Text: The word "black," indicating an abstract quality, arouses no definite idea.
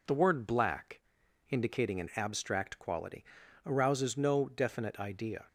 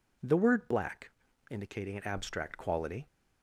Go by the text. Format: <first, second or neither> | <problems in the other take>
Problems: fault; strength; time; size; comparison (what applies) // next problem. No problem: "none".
first | stops before "arouses no definite idea"; at 3.0 s